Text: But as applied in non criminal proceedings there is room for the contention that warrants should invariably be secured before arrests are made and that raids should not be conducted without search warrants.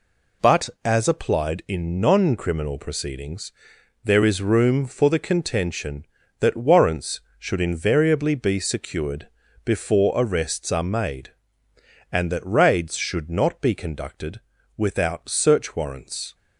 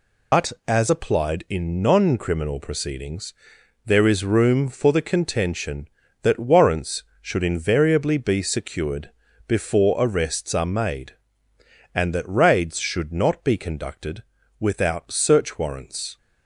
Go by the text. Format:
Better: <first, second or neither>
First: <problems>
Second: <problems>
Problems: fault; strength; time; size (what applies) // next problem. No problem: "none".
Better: first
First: pauses between "proceedings" and "there"; noticeable; at 3.5 s; 0.52 s long // pauses between "secured" and "before"; at 9.2 s; 0.38 s long // pauses between "conducted" and "without"; slight; at 14.4 s; 0.36 s long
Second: loses the start of "But"; at 0.3 s; 80 ms // pauses between "proceedings" and "there"; noticeable; at 3.3 s; 0.52 s long // pauses between "secured" and "before"; at 9.0 s; 0.38 s long // pauses between "conducted" and "without"; slight; at 14.2 s; 0.36 s long